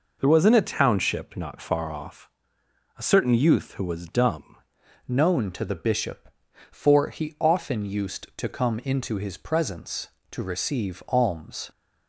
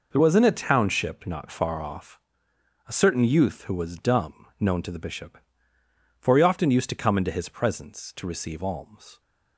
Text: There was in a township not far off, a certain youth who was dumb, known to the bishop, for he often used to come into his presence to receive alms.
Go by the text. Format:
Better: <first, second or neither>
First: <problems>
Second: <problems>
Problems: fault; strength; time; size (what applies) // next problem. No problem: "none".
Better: second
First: changes voice at "known"; from 5.0 s on; 6.6 s long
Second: none